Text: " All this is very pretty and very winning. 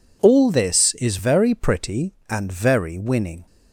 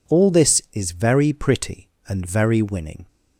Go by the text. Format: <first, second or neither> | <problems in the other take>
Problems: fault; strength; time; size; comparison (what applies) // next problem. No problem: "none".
neither | none